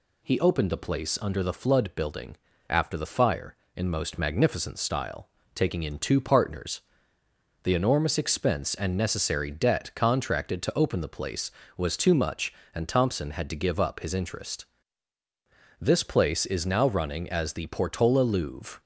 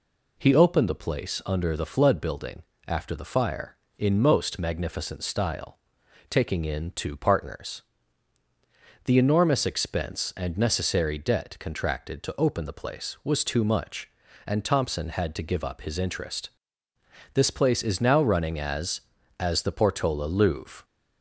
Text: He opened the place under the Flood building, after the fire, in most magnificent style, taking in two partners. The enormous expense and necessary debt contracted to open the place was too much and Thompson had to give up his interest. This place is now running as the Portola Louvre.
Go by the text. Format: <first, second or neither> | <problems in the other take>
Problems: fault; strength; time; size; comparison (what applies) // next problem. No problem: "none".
first | says "as" twice; at 19.4 s